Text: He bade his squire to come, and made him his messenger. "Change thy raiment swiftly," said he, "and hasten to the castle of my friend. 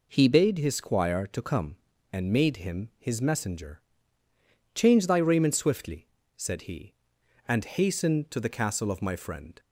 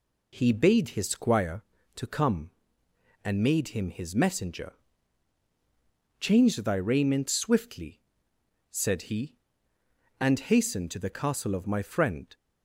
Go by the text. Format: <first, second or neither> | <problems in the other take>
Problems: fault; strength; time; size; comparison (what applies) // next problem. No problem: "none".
neither | none